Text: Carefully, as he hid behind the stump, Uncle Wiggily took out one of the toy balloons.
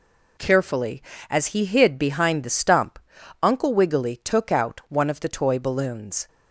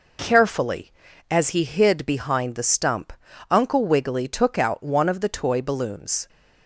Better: neither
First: none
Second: none

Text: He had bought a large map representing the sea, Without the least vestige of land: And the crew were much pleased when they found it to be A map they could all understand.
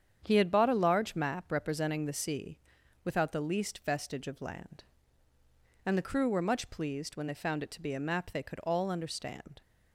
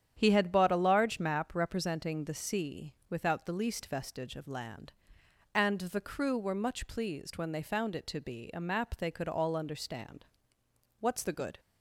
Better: first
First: starts louder than the rest; strong; until 1.2 s; 8.5 dB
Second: starts louder than the rest; strong; until 1.1 s; 9.5 dB // goes on to say "What's the good"; noticeable; from 10.9 s on; 0.62 s long

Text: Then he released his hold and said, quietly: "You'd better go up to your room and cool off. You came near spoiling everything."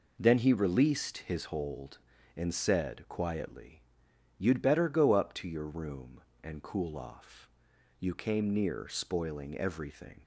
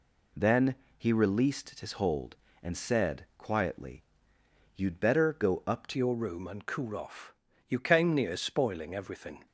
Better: first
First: none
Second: pauses between "Then" and "he"; slight; at 0.7 s; 0.22 s long // changes voice at "your"; from 5.9 s on; 3.5 s long

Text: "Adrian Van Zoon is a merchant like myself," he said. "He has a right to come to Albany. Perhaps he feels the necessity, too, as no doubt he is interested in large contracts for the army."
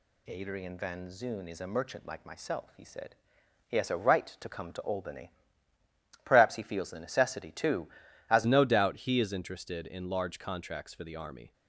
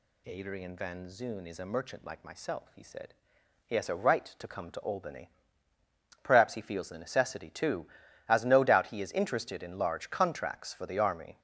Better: second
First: changes voice at "no"; from 8.4 s on; 3.1 s long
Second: none

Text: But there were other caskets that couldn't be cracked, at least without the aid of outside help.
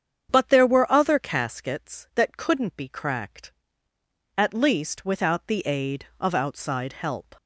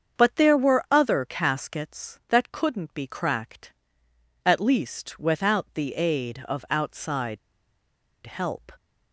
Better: first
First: starts louder than the rest; strong; until 1.3 s; 8 dB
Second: starts louder than the rest; strong; until 1.2 s; 7 dB // pauses between "outside" and "help"; noticeable; at 7.3 s; 0.87 s long

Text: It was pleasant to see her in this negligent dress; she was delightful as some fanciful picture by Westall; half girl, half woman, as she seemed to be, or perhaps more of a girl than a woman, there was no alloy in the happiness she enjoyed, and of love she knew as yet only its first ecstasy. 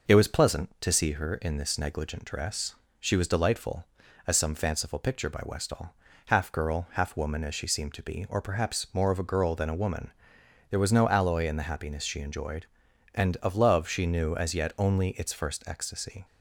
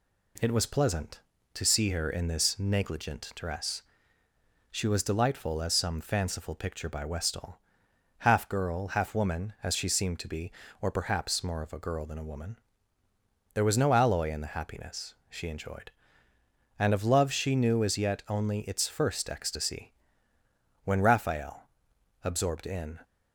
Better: first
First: none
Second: pauses between "happiness" and "she"; slight; at 15.1 s; 0.16 s long // goes on to say "When Raphael absorbed in"; strong; from 20.8 s on; 2.1 s long

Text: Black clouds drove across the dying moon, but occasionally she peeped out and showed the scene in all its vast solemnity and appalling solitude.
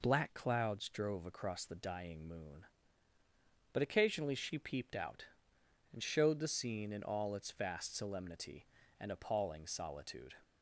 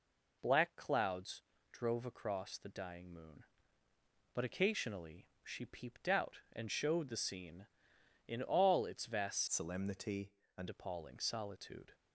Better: first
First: none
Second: pauses between "clouds" and "drove"; slight; at 1.4 s; 0.32 s long // pauses between "occasionally" and "she"; slight; at 5.2 s; 0.16 s long // changes voice from "solemnity" to "and"; from 9.5 to 10.6 s; 1.1 s long

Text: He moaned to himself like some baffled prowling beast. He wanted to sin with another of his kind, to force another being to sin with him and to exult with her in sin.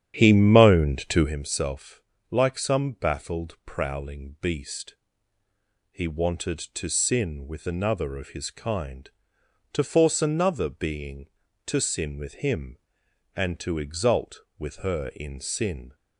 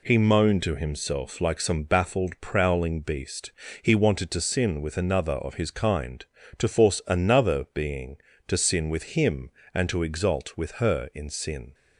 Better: second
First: starts louder than the rest; strong; until 1.4 s; 9.5 dB // pauses between "himself" and "like"; slight; at 2.0 s; 0.30 s long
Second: none

